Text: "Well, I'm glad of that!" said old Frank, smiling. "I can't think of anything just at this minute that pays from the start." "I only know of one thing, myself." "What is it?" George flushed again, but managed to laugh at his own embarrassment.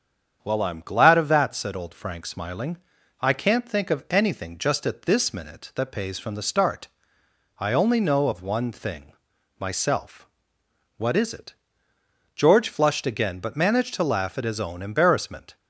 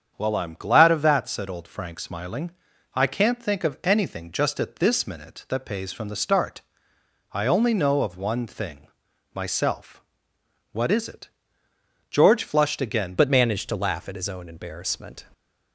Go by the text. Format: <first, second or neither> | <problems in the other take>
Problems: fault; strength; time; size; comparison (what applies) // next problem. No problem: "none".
first | starts louder than the rest; strong; until 1.1 s; 7.5 dB; strong in the first // changes voice at "but"; from 13.1 s on; 2.1 s long